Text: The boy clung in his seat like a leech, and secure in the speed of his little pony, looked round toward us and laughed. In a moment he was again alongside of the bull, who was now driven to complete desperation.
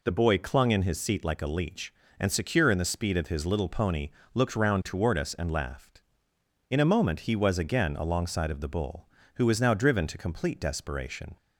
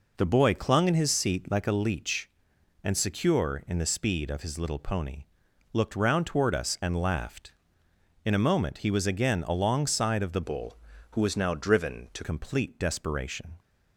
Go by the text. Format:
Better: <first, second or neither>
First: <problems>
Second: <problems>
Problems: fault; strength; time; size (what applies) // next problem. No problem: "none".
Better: first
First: none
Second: changes voice from "bull" to "to"; from 10.4 to 12.2 s; 1.8 s long